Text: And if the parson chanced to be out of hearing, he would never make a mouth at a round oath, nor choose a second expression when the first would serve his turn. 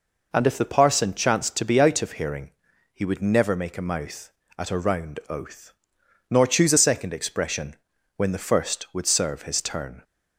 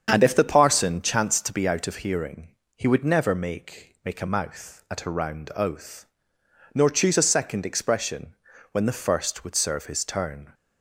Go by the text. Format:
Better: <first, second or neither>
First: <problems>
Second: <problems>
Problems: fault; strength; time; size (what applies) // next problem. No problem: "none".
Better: first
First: pauses between "expression" and "when"; at 7.7 s; 0.42 s long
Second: starts louder than the rest; strong; until 1.1 s; 7.5 dB // says "make" twice; at 4.0 s // pauses between "expression" and "when"; at 8.3 s; 0.38 s long